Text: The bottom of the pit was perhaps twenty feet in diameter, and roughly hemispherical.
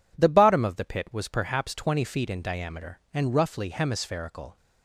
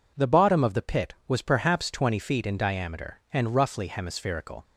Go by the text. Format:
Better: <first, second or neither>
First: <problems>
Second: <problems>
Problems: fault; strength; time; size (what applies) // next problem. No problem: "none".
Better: neither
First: none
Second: none